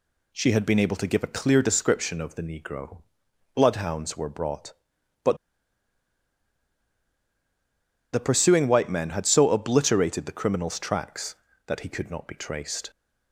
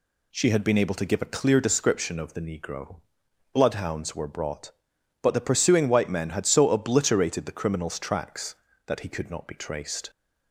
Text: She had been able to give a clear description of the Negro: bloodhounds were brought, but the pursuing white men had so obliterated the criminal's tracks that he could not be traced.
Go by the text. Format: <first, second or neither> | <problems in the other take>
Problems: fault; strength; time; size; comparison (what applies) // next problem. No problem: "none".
second | pauses between "but" and "the"; strong; at 5.3 s; 2.7 s long